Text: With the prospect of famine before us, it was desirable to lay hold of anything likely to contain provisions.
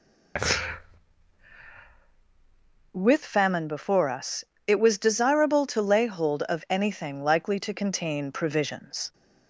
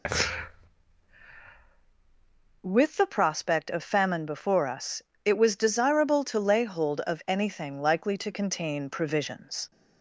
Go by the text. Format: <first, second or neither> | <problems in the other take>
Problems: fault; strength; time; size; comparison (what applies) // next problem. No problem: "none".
second | skips "the prospect of"; at 3.2 s